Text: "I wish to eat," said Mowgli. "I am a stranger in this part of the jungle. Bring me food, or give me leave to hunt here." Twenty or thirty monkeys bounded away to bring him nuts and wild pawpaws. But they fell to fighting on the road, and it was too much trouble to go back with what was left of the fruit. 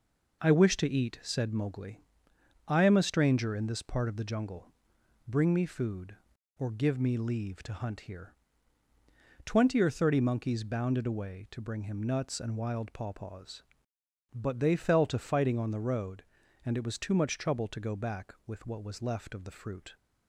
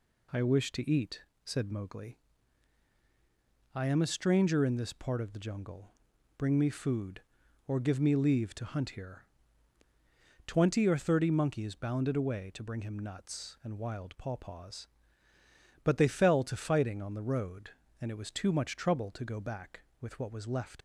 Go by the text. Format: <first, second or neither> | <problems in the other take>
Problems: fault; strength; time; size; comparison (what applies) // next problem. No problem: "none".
first | stops before "of the fruit"; at 20.7 s